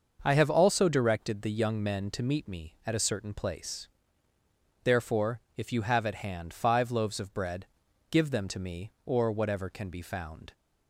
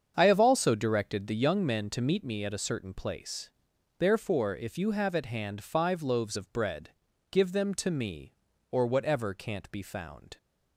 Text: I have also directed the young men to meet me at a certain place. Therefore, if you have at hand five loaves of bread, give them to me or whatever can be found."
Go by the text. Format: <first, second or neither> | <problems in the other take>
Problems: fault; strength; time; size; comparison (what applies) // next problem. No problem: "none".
first | starts louder than the rest; strong; until 1.1 s; 7.5 dB; also in the first // says "can't" for "can"; at 9.3 s